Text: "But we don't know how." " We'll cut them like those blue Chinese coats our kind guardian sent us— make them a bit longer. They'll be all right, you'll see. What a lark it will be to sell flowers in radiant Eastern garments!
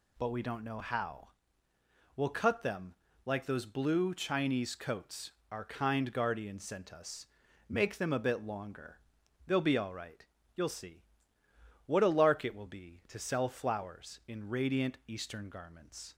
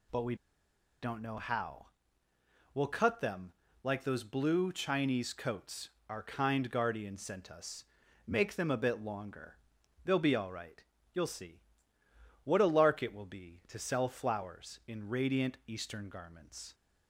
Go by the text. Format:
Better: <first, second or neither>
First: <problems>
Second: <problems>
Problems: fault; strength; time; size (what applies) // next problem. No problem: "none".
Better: first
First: pauses between "them" and "like"; slight; at 2.9 s; 0.32 s long // pauses between "coats" and "our"; slight; at 5.3 s; 0.18 s long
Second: pauses between "we" and "don't"; noticeable; at 0.3 s; 0.67 s long // pauses between "them" and "like"; slight; at 3.5 s; 0.32 s long // pauses between "coats" and "our"; slight; at 5.9 s; 0.18 s long